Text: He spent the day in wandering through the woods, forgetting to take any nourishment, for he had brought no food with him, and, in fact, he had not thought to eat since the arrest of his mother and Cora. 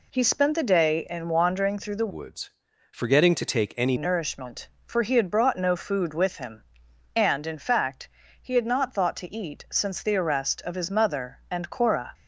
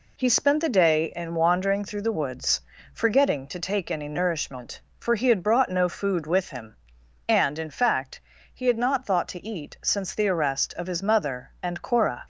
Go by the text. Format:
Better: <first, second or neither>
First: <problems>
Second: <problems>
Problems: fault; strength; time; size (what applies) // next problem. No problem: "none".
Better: second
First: changes voice from "woods" to "any"; from 2.0 to 3.9 s; 1.9 s long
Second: none